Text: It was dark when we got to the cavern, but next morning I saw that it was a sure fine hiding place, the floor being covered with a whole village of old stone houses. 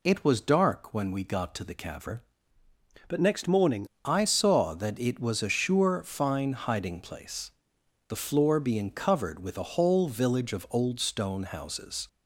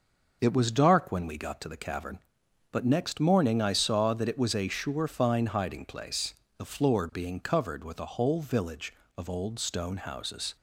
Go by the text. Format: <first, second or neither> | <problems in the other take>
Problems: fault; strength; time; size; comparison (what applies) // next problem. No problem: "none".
second | changes voice from "but" to "morning"; from 3.0 to 3.8 s; 0.8 s long